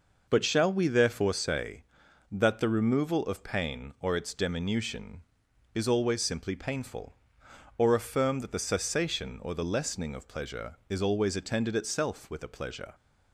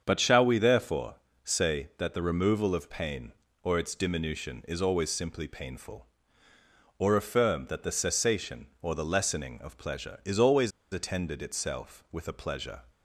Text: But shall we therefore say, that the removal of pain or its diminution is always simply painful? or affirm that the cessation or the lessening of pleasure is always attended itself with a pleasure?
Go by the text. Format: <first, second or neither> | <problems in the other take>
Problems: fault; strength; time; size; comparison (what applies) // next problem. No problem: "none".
first | starts louder than the rest; strong; until 1.0 s; 7.5 dB // pauses between "therefore" and "say"; slight; at 1.1 s; 0.30 s long // pauses between "always" and "attended"; slight; at 10.7 s; 0.21 s long